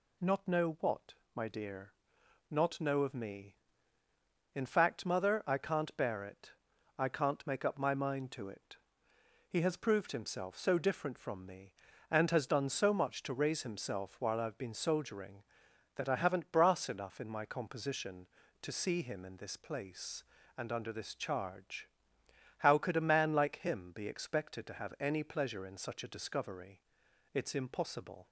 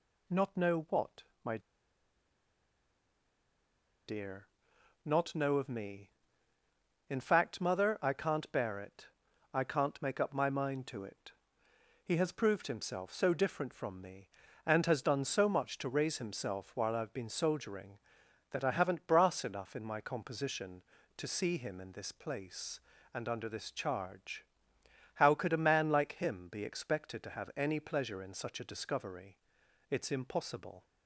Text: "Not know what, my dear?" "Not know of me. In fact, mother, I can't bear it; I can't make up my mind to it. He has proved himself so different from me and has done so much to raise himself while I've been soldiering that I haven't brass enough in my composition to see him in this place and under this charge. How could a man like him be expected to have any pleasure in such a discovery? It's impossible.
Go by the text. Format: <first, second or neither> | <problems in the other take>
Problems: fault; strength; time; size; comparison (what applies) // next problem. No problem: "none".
first | pauses between "my" and "dear"; strong; at 1.5 s; 2.4 s long